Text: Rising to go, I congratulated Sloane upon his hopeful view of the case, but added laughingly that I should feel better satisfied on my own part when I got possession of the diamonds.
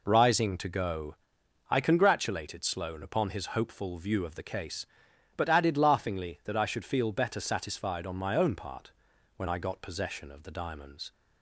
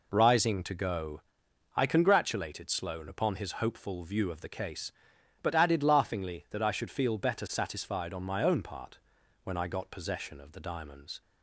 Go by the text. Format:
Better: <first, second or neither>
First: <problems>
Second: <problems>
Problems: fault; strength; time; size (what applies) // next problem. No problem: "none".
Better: neither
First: pauses between "part" and "when"; noticeable; at 8.9 s; 0.46 s long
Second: pauses between "part" and "when"; noticeable; at 8.9 s; 0.46 s long